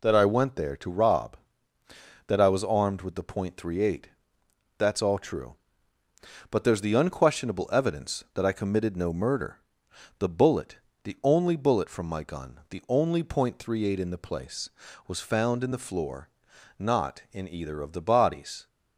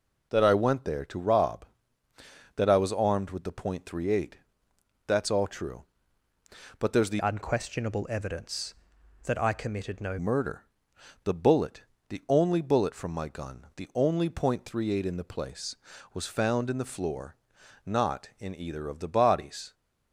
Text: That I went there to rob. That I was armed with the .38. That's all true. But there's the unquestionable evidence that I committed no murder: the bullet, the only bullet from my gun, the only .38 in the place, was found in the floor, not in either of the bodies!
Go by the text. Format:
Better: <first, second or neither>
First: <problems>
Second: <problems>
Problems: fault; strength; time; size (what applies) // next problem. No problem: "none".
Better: first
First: none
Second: changes voice from "unquestionable" to "no"; from 7.1 to 10.1 s; 3.0 s long